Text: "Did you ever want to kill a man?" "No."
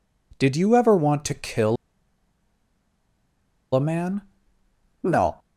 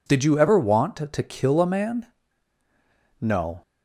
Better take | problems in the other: second | pauses between "kill" and "a"; strong; at 1.7 s; 1.9 s long

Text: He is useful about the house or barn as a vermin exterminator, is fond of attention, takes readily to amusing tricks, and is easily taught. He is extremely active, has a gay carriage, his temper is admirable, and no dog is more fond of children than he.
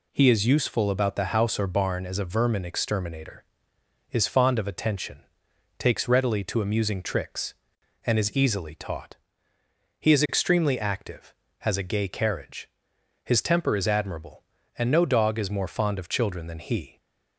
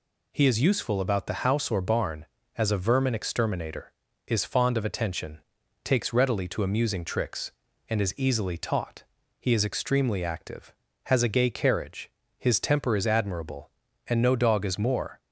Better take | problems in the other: first | stops before "fond of children than he"; at 15.1 s

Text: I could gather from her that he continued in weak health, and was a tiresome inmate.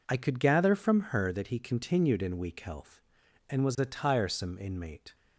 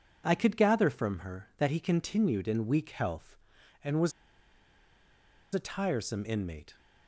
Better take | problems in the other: first | pauses between "was" and "a"; strong; at 4.1 s; 1.4 s long

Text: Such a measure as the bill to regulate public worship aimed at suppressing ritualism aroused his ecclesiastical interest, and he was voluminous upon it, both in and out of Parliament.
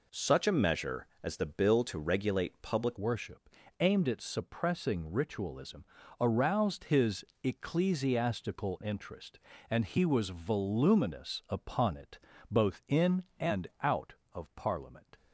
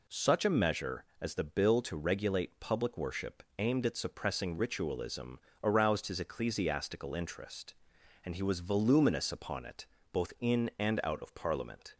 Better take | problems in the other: second | changes voice at "worship"; from 2.9 s on; 12.2 s long // pauses between "worship" and "aimed"; slight; at 3.4 s; 0.32 s long; slight in the second // pauses between "ritualism" and "aroused"; at 5.8 s; 0.38 s long; slight in the second // pauses between "his" and "ecclesiastical"; slight; at 7.2 s; 0.18 s long

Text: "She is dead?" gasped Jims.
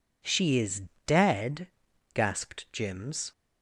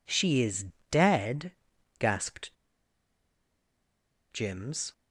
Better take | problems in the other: first | pauses between "is" and "dead"; slight; at 0.6 s; 0.22 s long; slight in the first // pauses between "gasped" and "Jims"; strong; at 2.5 s; 1.7 s long

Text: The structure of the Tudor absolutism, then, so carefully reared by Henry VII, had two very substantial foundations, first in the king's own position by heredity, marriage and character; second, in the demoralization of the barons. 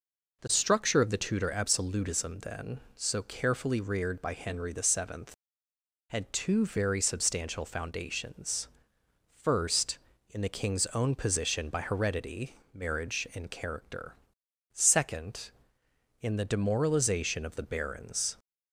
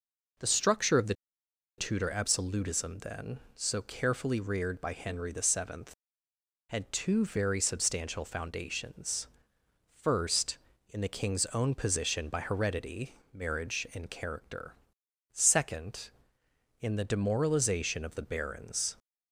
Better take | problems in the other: first | pauses between "the" and "Tudor"; noticeable; at 1.1 s; 0.64 s long

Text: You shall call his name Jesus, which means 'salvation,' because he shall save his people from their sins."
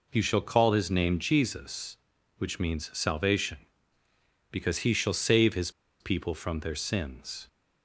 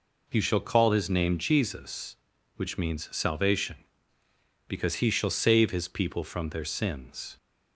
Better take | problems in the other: second | pauses between "his" and "people"; slight; at 5.6 s; 0.30 s long

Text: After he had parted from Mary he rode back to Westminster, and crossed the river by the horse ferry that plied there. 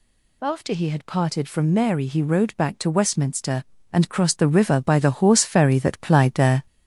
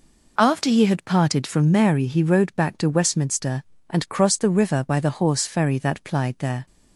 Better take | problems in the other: second | gets louder; throughout; 3.5 dB

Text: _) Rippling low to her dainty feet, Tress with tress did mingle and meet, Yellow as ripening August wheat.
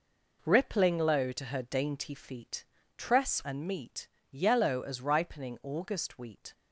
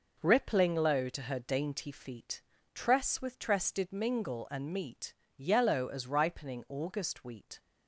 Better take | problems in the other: second | skips "with tress did mingle"; at 3.4 s

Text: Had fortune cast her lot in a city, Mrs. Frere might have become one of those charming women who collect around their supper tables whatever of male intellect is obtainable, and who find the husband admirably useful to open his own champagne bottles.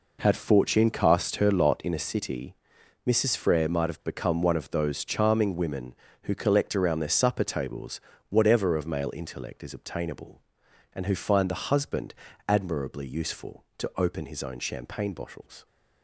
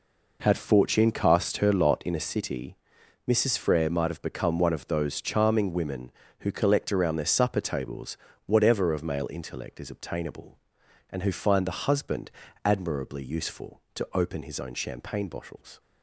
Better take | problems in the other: neither | pauses between "tables" and "whatever"; slight; the same in both // pauses between "husband" and "admirably"; slight; the same in both

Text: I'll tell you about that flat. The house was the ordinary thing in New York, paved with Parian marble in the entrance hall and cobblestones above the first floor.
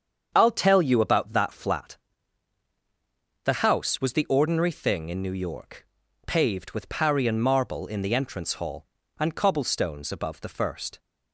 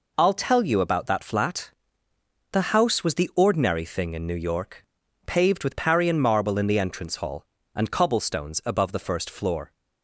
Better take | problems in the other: second | starts louder than the rest; strong; until 1.3 s; 7.5 dB // stops before "floor"; at 10.9 s

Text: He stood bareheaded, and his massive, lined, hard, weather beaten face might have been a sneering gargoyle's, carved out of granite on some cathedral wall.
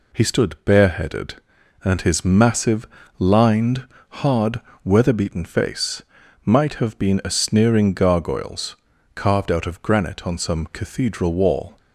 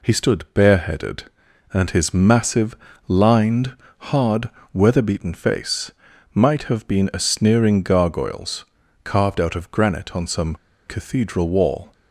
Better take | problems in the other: first | pauses between "face" and "might"; at 5.9 s; 0.42 s long; also in the first // pauses between "some" and "cathedral"; slight; at 10.5 s; 0.29 s long

